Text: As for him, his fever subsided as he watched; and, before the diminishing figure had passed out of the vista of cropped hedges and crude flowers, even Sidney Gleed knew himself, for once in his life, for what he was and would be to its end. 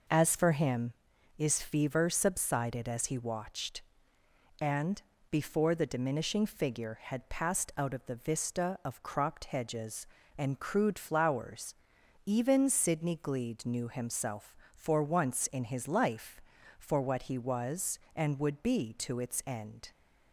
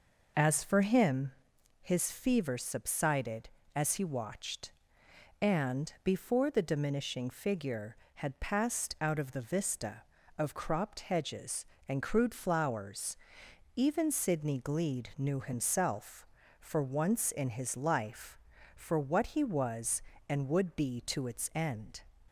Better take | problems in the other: neither | none

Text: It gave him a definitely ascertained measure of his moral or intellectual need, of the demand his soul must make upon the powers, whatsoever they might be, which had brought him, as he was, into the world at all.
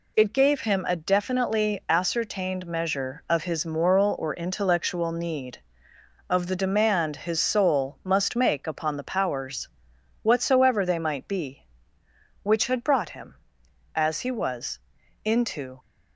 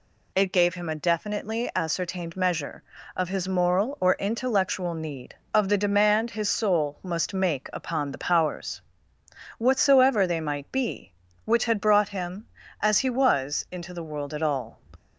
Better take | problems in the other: second | stops before "the world at all"; at 15.8 s

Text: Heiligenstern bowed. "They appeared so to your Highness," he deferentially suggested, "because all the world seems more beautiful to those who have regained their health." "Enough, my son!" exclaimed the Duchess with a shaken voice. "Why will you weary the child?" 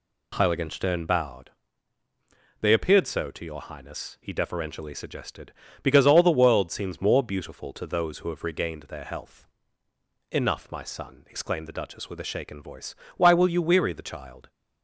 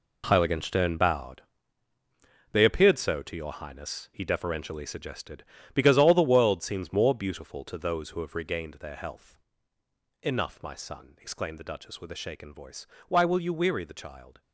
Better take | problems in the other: first | gets quieter; strong; throughout; 11 dB

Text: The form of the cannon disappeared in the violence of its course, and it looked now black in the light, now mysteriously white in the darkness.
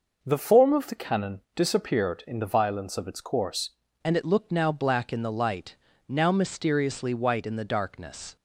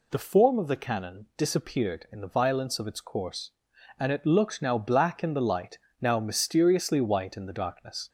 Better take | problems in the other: second | changes voice at "and"; from 4.0 s on; 4.3 s long

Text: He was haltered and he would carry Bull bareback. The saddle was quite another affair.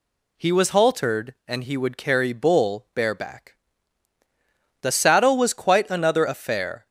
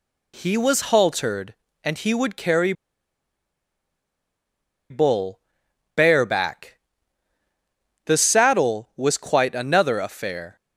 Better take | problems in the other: first | pauses between "carry" and "Bull"; strong; at 2.7 s; 2.1 s long // pauses between "Bull" and "bareback"; noticeable; at 5.3 s; 0.54 s long

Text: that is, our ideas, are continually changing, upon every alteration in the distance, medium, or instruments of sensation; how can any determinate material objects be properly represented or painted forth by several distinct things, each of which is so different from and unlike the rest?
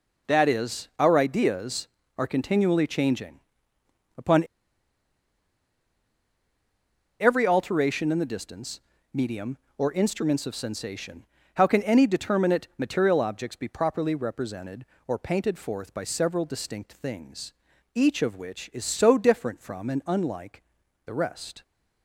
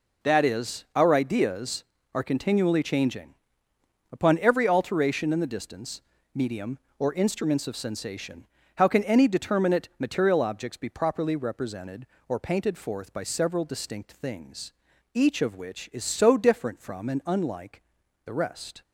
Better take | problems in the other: second | pauses between "upon" and "every"; strong; at 4.4 s; 2.7 s long // pauses between "unlike" and "the"; at 20.6 s; 0.44 s long; also in the second

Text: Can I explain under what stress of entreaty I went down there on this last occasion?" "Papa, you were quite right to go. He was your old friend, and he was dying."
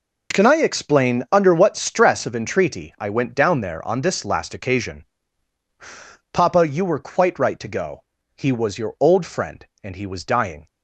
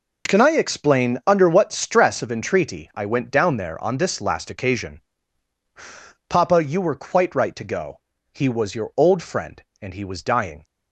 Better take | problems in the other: neither | none

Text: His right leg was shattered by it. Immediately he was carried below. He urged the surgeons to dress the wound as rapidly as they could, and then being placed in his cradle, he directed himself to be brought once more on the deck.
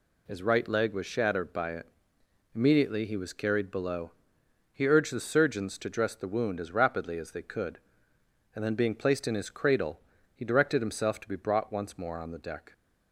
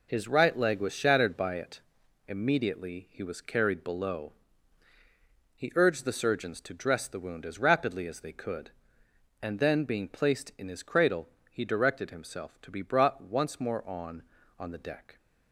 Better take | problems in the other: first | says "on" twice; at 14.5 s

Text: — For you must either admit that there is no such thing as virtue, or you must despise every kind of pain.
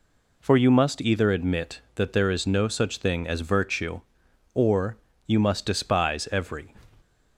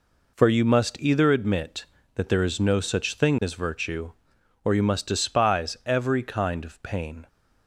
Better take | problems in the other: second | pauses between "or" and "you"; slight; at 4.9 s; 0.30 s long // stops before "kind of pain"; at 7.0 s

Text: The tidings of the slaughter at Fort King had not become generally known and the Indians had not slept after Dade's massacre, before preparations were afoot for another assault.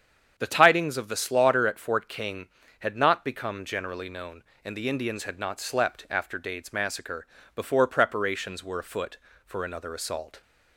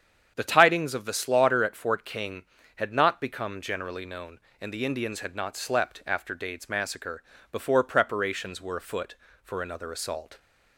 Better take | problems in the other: neither | starts louder than the rest; strong; the same in both

